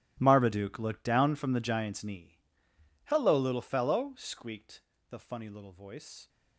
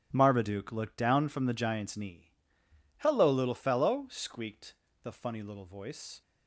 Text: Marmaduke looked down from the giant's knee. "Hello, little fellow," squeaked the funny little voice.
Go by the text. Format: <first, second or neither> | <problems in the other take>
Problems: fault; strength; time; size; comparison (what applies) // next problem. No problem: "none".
second | gets quieter; strong; throughout; 16 dB // starts louder than the rest; strong; until 1.2 s; 11 dB; strong in the second // pauses between "squeaked" and "the"; slight; at 4.8 s; 0.28 s long; slight in the second